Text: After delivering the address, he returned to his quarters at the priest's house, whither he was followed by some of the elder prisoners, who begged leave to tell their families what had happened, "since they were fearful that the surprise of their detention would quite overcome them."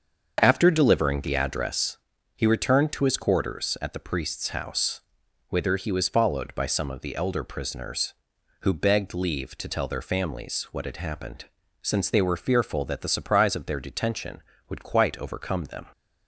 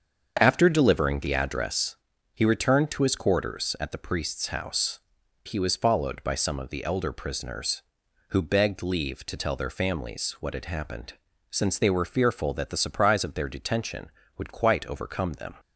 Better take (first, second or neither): first